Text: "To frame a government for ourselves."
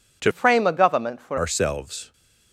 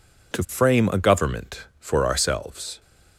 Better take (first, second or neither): second